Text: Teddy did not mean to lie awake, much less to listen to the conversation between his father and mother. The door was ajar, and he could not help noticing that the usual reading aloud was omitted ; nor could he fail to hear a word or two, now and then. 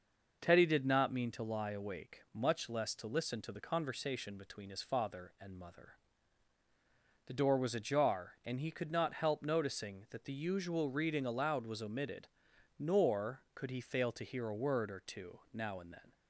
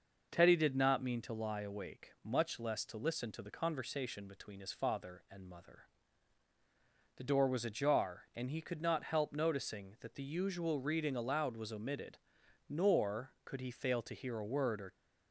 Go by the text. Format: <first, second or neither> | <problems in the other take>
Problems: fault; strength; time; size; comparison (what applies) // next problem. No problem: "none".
first | stops before "two now and then"; at 14.9 s